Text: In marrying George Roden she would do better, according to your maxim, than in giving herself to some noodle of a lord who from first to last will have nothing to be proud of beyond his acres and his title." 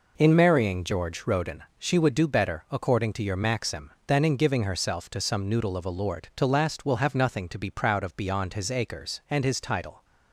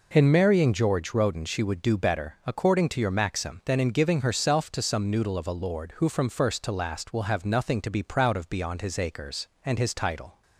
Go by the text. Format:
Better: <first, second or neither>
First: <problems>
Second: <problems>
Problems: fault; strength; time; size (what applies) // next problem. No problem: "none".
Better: second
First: pauses between "Roden" and "she"; slight; at 1.6 s; 0.16 s long // skips "who from first"; at 6.3 s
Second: none